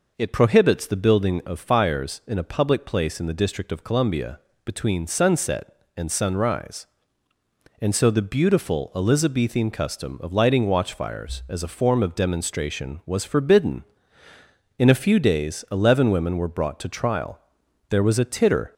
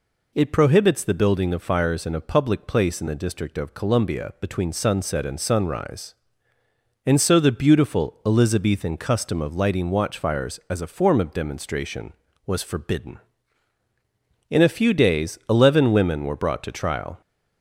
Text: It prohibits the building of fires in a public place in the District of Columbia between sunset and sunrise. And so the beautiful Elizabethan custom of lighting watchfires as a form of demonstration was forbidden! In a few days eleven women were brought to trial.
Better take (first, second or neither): second